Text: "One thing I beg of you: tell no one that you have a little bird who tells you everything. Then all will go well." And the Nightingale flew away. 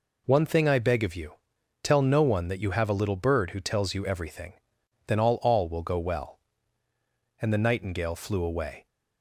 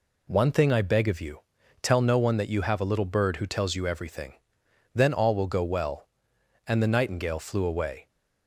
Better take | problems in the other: second | says "all" twice; at 5.4 s

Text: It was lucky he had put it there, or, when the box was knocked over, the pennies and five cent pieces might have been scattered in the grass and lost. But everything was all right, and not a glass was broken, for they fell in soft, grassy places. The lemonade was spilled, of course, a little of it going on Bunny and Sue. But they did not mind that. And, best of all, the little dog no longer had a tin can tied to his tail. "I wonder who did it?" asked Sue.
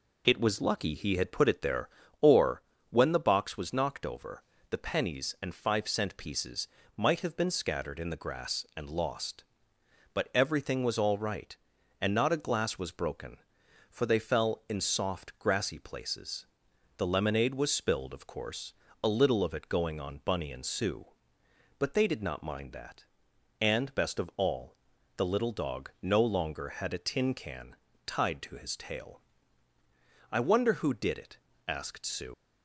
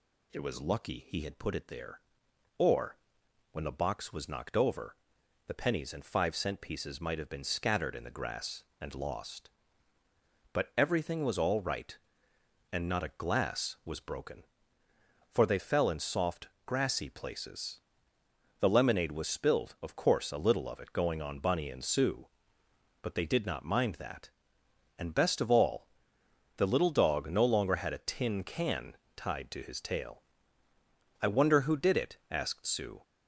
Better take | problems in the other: second | pauses between "pieces" and "might"; slight; at 6.6 s; 0.30 s long // pauses between "can" and "tied"; slight; at 27.7 s; 0.30 s long; slight in the second // leaves "Sue" unfinished; at 32.3 s; 95 ms

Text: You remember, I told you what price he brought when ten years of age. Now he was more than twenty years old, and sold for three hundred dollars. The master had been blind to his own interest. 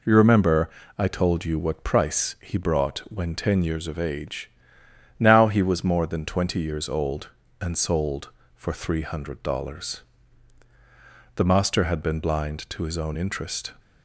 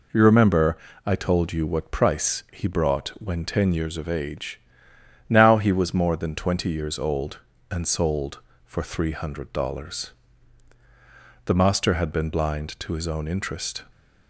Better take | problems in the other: neither | none

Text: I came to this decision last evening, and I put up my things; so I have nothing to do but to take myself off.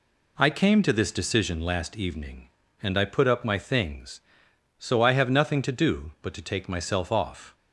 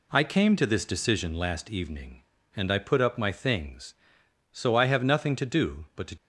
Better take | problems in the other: first | stops before "take myself off"; at 6.1 s

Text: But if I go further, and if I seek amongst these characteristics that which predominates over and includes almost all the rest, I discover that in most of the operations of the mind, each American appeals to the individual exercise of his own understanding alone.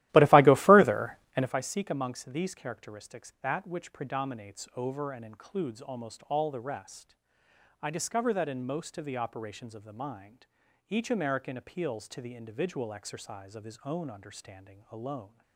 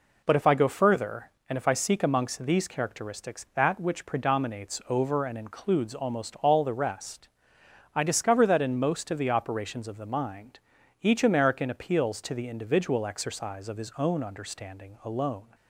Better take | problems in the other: second | starts louder than the rest; strong; until 1.5 s; 15.5 dB

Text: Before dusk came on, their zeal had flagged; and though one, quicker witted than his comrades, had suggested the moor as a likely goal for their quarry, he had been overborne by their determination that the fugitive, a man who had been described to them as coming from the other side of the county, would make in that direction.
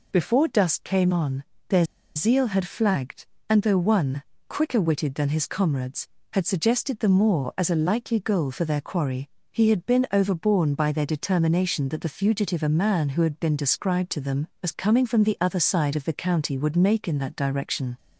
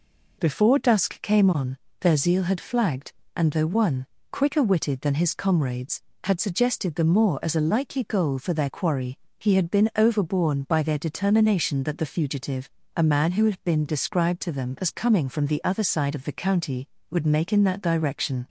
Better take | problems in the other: second | pauses between "their" and "zeal"; slight; at 1.8 s; 0.32 s long

